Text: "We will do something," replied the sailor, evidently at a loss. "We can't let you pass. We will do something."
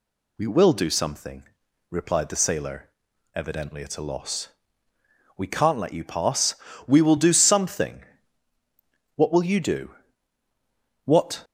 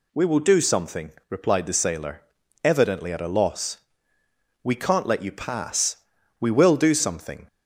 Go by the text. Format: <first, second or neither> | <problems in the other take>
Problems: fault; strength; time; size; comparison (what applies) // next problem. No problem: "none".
second | goes on to say "What will you do What"; strong; from 9.1 s on; 2.2 s long